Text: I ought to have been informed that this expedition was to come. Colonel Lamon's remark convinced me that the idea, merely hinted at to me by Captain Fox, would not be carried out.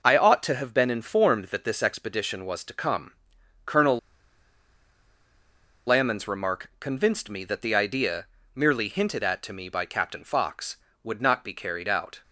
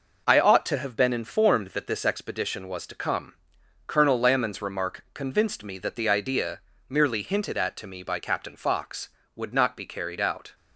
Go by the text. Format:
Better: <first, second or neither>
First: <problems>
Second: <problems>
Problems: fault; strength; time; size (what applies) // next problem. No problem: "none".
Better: second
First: pauses between "Colonel" and "Lamon's"; strong; at 3.9 s; 1.8 s long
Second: none